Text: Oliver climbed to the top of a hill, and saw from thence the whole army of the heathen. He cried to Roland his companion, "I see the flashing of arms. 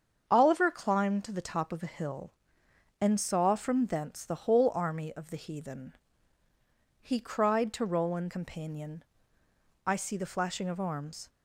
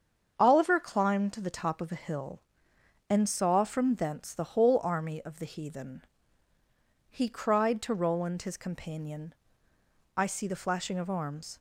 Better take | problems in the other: second | starts louder than the rest; strong; until 1.2 s; 7.5 dB; strong in the second // skips "his"; at 8.2 s

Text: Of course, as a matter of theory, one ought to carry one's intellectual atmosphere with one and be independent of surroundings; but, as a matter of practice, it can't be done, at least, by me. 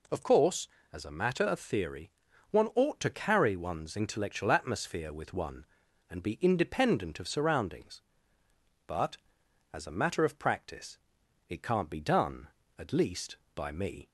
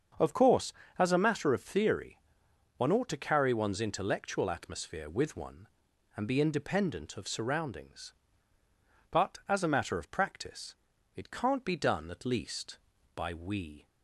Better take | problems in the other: first | starts louder than the rest; until 1.4 s; 6.5 dB // says "we" for "me"; at 13.3 s

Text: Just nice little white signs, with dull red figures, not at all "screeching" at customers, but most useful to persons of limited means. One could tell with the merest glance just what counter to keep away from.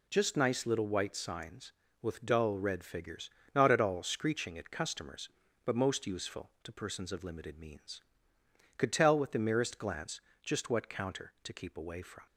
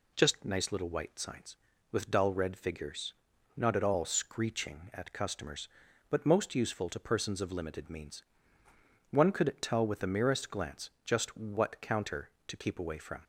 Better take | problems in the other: second | skips "One"; at 8.3 s // pauses between "glance" and "just"; slight; at 10.1 s; 0.24 s long

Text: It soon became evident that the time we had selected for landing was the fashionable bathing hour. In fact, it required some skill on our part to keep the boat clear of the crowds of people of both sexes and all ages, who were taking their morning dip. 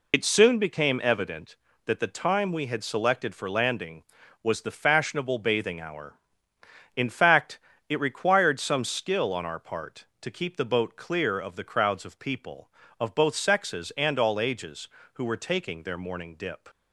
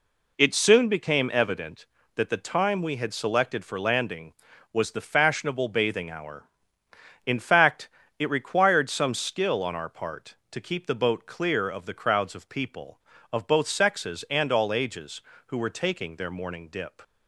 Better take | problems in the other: second | loses the start of "It"; at 0.1 s; 75 ms

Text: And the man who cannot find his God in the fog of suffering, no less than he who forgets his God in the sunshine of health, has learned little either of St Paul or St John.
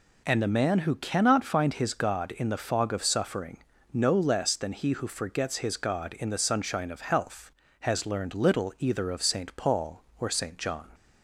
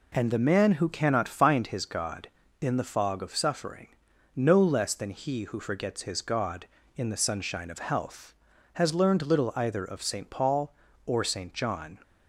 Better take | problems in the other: neither | none

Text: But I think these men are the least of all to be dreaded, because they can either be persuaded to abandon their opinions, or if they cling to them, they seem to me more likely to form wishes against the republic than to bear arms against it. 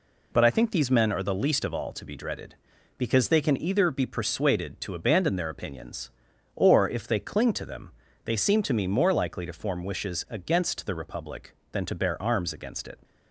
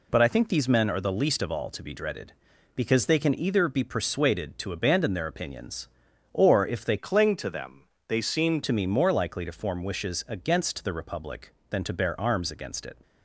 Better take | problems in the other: first | changes voice from "cling" to "seem"; from 6.9 to 8.6 s; 1.7 s long

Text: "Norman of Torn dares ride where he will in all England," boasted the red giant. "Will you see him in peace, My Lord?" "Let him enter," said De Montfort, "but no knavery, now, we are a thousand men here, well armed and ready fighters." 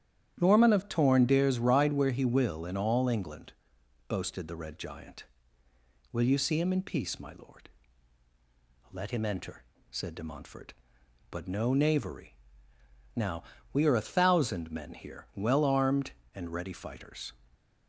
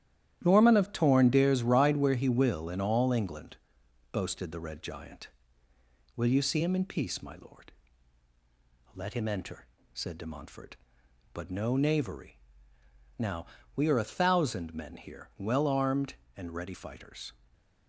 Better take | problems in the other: first | gets quieter; strong; throughout; 8 dB // starts louder than the rest; strong; until 1.4 s; 11 dB; strong in the first // stays silent after the last word; slight; from 17.3 s on; 0.5 s long

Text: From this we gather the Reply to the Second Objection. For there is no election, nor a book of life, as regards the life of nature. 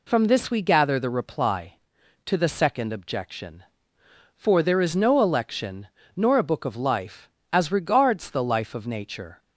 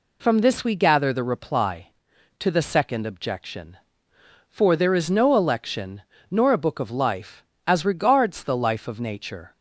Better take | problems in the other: neither | none

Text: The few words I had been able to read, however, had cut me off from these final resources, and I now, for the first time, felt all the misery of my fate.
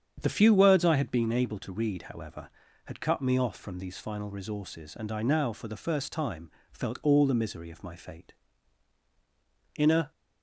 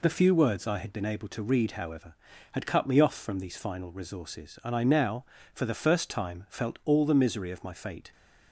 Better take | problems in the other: second | starts louder than the rest; strong; until 1.2 s; 8 dB // goes on to say "In a"; slight; from 9.7 s on; 0.34 s long

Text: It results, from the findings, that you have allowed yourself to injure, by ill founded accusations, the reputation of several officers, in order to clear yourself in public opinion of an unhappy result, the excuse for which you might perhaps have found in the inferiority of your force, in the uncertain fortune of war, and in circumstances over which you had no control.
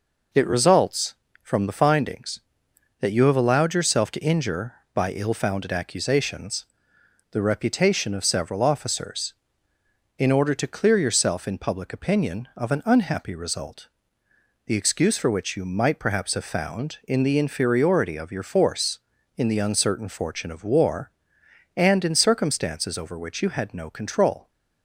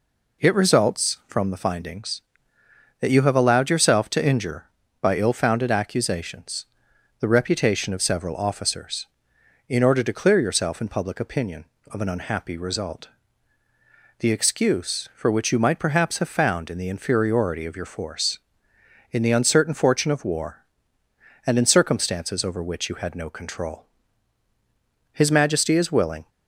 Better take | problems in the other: first | goes on to say "His Majesty is willing"; noticeable; from 25.1 s on; 1.1 s long

